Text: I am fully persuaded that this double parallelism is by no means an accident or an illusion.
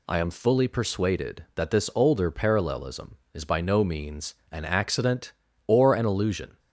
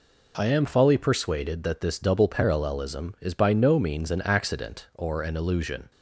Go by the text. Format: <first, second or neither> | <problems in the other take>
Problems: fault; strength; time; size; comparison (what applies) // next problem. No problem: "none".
second | says "older" for "double"; at 1.9 s // pauses between "means" and "an"; slight; at 4.3 s; 0.18 s long